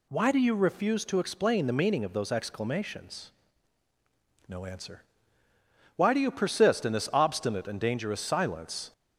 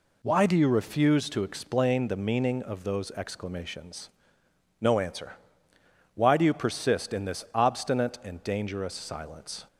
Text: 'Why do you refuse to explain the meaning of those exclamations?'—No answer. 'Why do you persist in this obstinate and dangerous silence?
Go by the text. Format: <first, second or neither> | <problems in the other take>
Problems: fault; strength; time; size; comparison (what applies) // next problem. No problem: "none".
neither | none